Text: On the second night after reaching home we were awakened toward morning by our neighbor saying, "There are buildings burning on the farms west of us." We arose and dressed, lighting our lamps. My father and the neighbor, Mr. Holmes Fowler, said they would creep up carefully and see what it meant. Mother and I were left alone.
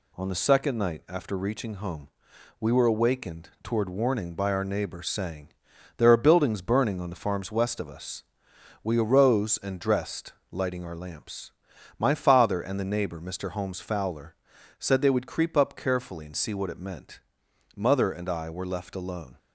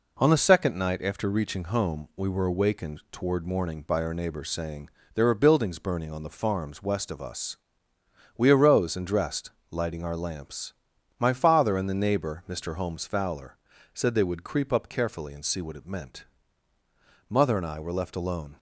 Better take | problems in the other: second | pauses between "home" and "we"; noticeable; at 2.0 s; 0.52 s long // says "warning" for "morning"; at 3.8 s

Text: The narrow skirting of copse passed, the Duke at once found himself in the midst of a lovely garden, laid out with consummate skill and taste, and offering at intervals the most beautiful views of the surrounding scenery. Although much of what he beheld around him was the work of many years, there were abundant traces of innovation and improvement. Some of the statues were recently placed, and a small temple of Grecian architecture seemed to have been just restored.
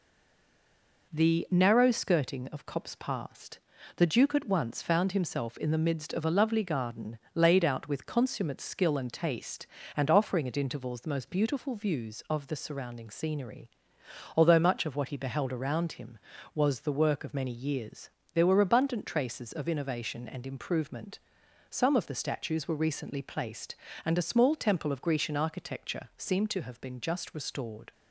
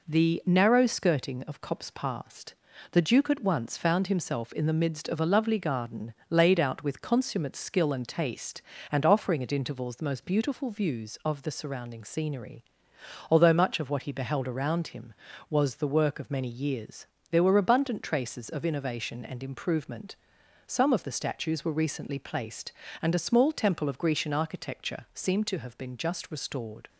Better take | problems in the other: second | stays silent before the first word; until 1.1 s; 1.1 s long

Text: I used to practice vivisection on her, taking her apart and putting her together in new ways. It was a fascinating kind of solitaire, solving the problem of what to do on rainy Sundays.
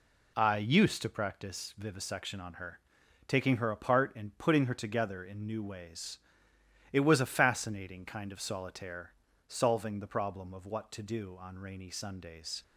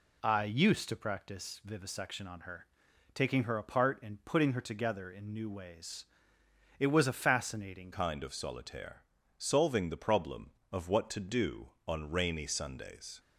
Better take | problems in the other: first | changes voice at "kind"; from 7.9 s on; 5.2 s long

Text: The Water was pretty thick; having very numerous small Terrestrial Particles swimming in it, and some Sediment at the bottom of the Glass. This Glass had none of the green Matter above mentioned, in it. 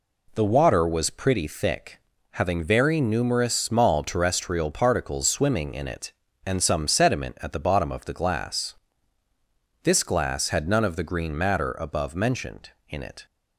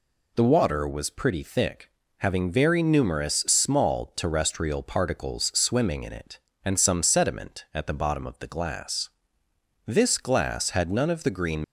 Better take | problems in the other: first | stops before "Matter above mentioned in it"; at 11.6 s

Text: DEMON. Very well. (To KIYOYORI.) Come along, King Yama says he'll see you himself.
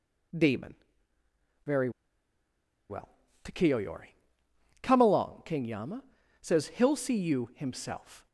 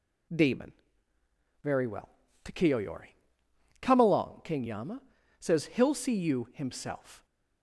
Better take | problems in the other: second | pauses between "Very" and "well"; at 1.8 s; 1.0 s long // pauses between "Yama" and "says"; at 6.0 s; 0.38 s long; also in the second

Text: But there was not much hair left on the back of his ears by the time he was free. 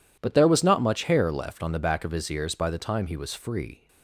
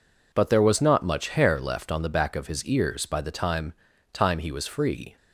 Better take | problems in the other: first | says "time" twice; at 4.1 s

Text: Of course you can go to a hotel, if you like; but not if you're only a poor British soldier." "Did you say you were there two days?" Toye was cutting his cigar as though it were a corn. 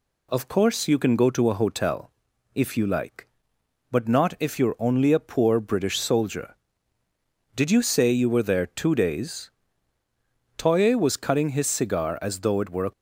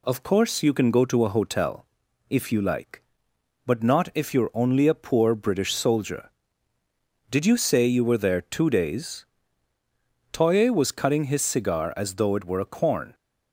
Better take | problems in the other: second | stops before "corn"; at 12.9 s

